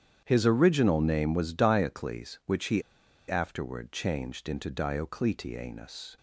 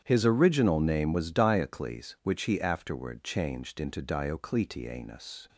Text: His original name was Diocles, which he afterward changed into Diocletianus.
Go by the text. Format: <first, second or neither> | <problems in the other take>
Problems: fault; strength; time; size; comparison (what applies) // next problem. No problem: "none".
second | starts louder than the rest; strong; until 1.2 s; 9 dB; strong in the second // pauses between "he" and "afterward"; noticeable; at 2.8 s; 0.47 s long